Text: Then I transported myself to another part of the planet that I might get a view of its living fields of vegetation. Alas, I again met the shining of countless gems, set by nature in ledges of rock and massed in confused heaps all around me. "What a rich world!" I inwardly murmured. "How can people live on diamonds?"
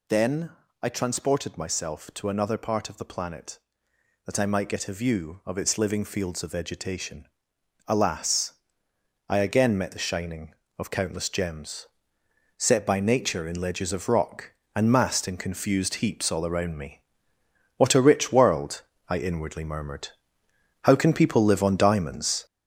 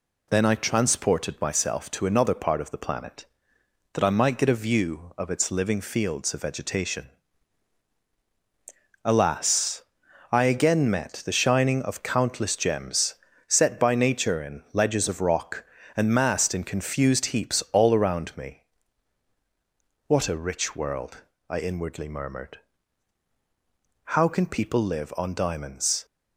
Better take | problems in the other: second | gets louder; noticeable; throughout; 5.5 dB // pauses between "Then" and "I"; slight; at 0.5 s; 0.30 s long

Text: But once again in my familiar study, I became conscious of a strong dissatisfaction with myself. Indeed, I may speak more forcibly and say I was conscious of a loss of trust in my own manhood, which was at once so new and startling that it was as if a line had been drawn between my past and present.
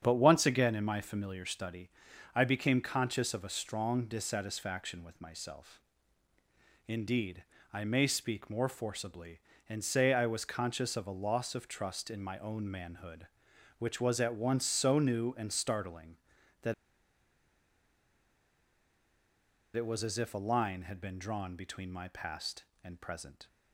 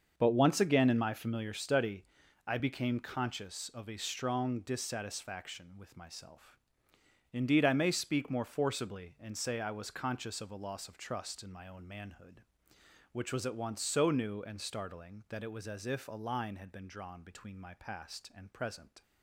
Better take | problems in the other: second | starts louder than the rest; strong; until 1.0 s; 8 dB; also in the second // pauses between "that" and "it"; strong; at 16.7 s; 3.0 s long

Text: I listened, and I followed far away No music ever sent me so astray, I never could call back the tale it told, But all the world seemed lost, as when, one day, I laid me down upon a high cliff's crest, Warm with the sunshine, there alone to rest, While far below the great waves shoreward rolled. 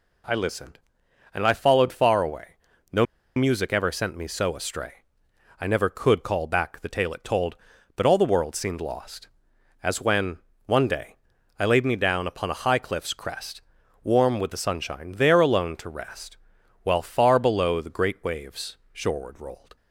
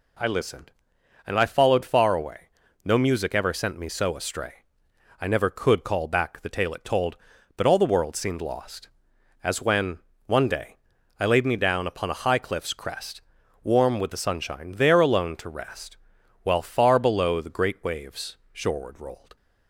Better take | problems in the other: second | pauses between "away" and "No"; slight; at 2.5 s; 0.36 s long; slight in the second // pauses between "No" and "music"; slight; at 3.0 s; 0.31 s long // pauses between "waves" and "shoreward"; slight; at 18.7 s; 0.16 s long; slight in the second

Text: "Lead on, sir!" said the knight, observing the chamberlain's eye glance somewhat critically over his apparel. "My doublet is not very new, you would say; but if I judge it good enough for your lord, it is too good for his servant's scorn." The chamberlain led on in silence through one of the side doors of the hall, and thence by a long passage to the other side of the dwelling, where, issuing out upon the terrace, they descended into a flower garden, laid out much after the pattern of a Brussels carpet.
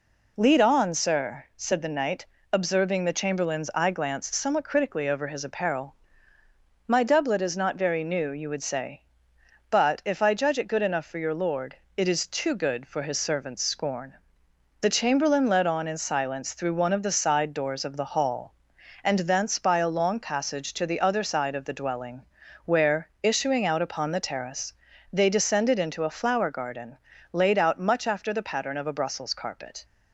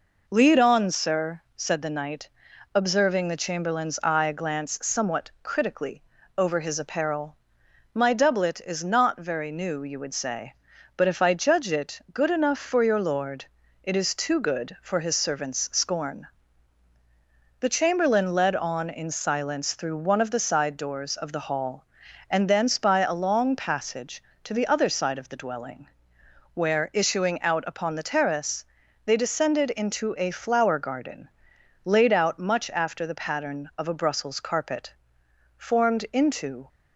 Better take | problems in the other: first | pauses between "critically" and "over"; slight; at 6.0 s; 0.34 s long // goes on to say "Formed into"; noticeable; from 35.5 s on; 1.1 s long

